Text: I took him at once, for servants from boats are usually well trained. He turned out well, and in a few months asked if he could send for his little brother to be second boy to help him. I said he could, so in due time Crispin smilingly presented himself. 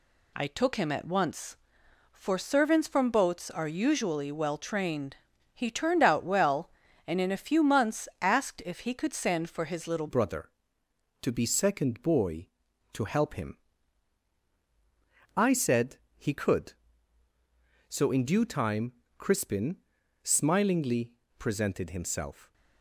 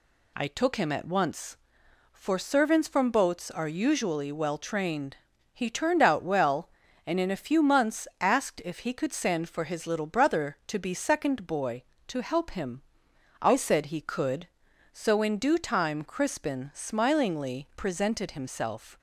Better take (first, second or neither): second